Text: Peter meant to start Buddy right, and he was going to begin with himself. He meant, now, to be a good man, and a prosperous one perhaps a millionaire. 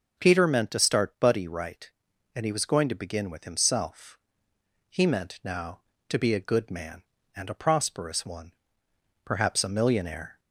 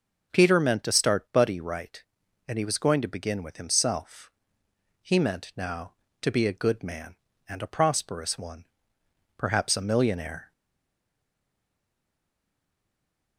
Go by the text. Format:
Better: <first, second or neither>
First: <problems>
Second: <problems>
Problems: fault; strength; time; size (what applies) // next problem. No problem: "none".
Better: first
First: pauses between "one" and "perhaps"; noticeable; at 8.5 s; 0.72 s long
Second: pauses between "one" and "perhaps"; noticeable; at 8.6 s; 0.72 s long // stays silent after the last word; strong; from 10.5 s on; 2.8 s long